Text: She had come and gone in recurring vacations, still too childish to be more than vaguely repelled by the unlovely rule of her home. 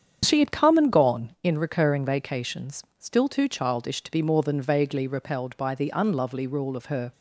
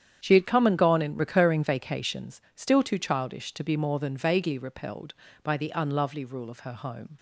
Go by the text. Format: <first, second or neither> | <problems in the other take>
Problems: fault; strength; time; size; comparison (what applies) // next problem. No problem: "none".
second | starts louder than the rest; strong; until 1.2 s; 8 dB; strong in the second // stops before "home"; at 7.1 s